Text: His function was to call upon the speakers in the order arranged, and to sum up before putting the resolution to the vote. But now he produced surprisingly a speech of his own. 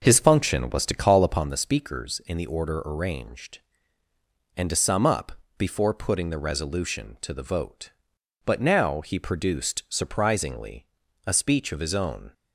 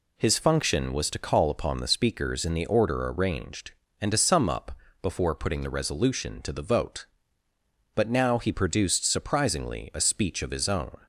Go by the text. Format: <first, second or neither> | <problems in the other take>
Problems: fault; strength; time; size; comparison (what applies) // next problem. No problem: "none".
second | starts louder than the rest; noticeable; until 1.5 s; 5.5 dB // pauses between "up" and "before"; slight; at 5.3 s; 0.26 s long; slight in the second // pauses between "surprisingly" and "a"; at 10.8 s; 0.38 s long